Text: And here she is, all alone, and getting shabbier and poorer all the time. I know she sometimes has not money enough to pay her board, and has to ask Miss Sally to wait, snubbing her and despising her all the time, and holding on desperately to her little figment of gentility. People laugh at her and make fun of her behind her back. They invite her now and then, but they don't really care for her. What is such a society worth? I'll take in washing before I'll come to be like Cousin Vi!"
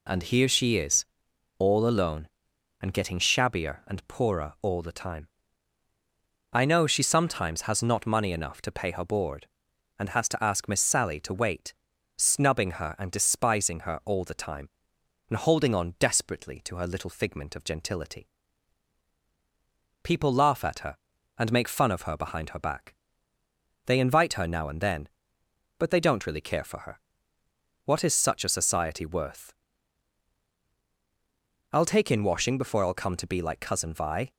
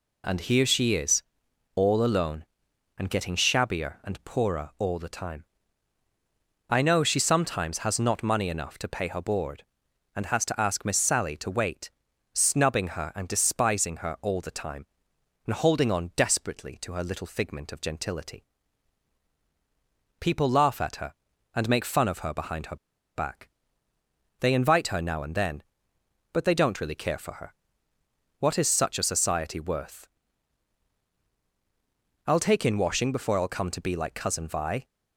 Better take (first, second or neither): first